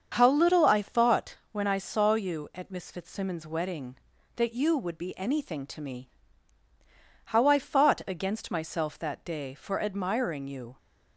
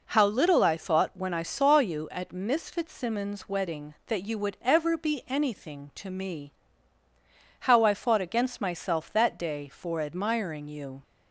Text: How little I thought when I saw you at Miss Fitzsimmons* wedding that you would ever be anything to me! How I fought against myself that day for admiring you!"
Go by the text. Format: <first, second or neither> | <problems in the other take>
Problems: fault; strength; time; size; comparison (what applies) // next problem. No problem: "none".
second | starts louder than the rest; until 1.1 s; 7 dB // pauses between "thought" and "when"; slight; at 1.3 s; 0.16 s long // skips "ever"; at 4.9 s